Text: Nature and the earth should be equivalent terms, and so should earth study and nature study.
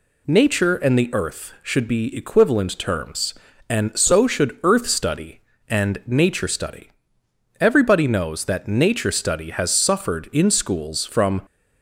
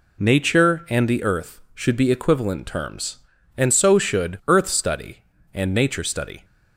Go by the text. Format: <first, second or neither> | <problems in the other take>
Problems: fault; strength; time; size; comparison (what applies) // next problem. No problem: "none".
second | goes on to say "Everybody knows that nature study has suffered in schools from"; strong; from 7.5 s on; 3.8 s long